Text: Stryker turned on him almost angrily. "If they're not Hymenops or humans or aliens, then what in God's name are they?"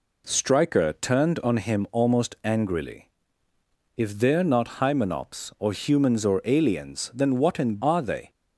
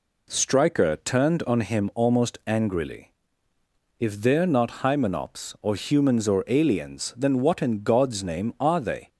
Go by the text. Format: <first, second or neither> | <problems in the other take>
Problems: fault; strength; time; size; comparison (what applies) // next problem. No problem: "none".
second | skips "God's name"; at 7.8 s